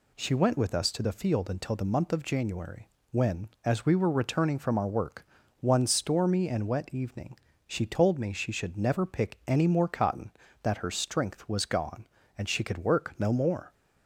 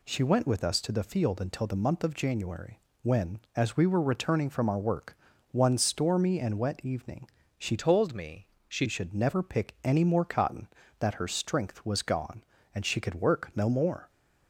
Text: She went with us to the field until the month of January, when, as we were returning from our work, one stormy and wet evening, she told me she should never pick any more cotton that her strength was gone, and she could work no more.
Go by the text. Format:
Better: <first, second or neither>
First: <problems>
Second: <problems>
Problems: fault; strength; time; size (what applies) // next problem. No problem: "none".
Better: first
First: none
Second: changes voice from "told" to "she"; from 7.7 to 8.8 s; 1.1 s long // pauses between "me" and "she"; slight; at 8.4 s; 0.18 s long